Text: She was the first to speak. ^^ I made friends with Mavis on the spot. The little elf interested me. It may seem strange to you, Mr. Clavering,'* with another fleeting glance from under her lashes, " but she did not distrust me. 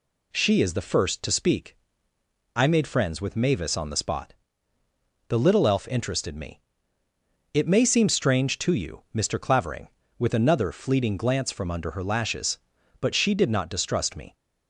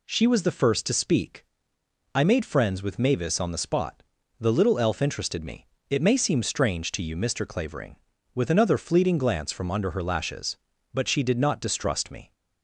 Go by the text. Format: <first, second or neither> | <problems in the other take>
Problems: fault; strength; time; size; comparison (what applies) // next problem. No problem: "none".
second | says "is" for "was"; at 0.6 s